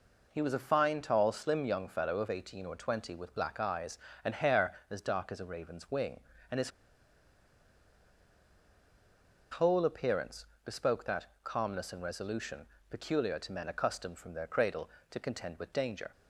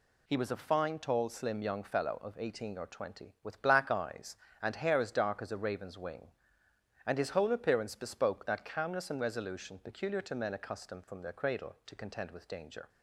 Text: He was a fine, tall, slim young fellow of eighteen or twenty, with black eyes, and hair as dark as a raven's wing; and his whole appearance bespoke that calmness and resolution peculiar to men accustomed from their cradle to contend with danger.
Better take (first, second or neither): second